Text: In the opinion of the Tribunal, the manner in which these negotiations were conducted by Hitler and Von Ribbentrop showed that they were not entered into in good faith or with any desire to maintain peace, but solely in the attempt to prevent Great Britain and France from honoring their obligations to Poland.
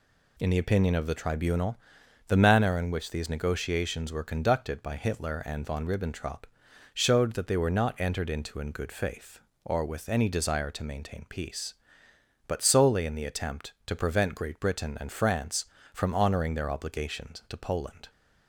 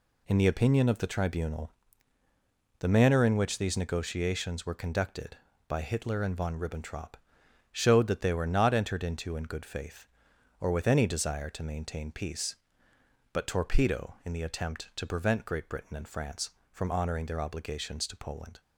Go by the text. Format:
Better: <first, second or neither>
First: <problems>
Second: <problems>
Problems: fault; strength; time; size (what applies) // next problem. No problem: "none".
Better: first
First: pauses between "Ribbentrop" and "showed"; noticeable; at 6.4 s; 0.50 s long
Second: pauses between "Ribbentrop" and "showed"; noticeable; at 7.1 s; 0.56 s long // says "torpedo" for "solely"; at 13.4 s